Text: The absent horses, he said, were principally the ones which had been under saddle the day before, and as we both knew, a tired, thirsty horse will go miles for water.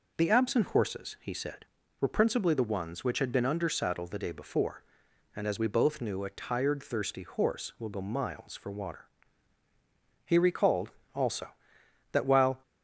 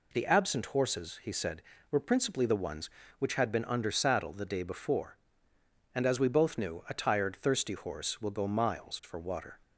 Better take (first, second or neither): second